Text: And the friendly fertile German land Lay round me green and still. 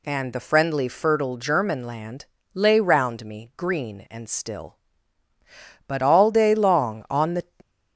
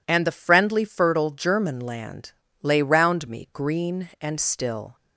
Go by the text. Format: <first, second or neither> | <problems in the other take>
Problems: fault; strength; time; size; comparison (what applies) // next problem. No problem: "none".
second | pauses between "land" and "Lay"; slight; at 2.2 s; 0.30 s long; slight in the second // goes on to say "But all day long on the"; from 5.8 s on; 1.5 s long